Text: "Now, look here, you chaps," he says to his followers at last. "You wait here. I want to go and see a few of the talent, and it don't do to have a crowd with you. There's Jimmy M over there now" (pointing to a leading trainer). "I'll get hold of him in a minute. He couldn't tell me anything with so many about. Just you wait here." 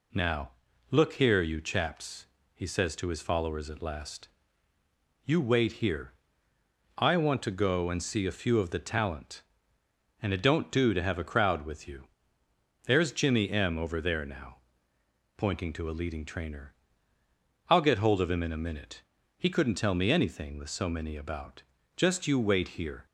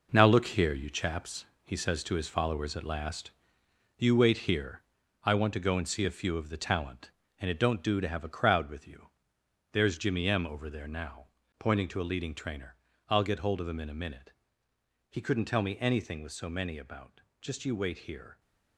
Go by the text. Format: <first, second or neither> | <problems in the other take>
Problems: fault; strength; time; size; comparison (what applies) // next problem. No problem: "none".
first | gets quieter; strong; throughout; 8 dB